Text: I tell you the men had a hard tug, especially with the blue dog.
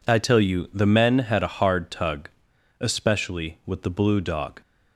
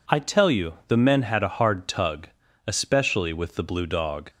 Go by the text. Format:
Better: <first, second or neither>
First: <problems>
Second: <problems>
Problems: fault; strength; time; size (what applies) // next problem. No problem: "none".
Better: neither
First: none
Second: none